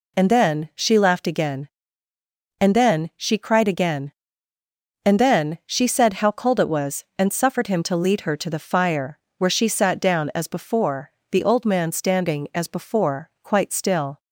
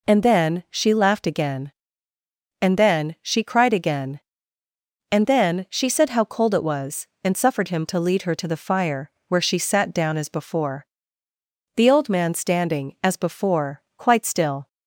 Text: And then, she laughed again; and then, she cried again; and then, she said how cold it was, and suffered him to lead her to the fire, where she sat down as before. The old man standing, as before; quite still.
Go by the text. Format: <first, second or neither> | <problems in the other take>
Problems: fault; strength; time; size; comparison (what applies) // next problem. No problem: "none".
neither | none